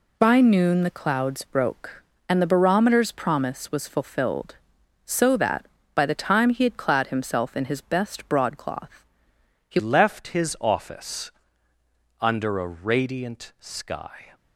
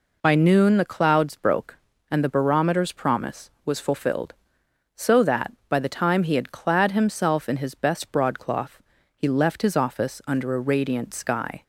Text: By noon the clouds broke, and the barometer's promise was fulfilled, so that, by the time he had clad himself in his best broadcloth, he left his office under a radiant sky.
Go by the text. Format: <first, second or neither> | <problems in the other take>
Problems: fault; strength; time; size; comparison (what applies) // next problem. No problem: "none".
second | changes voice at "left"; from 9.7 s on; 4.6 s long // pauses between "office" and "under"; noticeable; at 11.3 s; 0.90 s long